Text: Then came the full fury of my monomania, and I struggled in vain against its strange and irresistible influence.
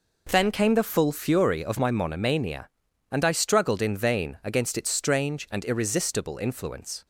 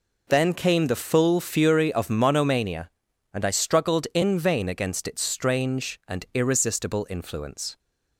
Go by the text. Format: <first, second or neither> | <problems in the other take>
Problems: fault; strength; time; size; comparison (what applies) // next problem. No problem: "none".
first | skips "my"; at 2.1 s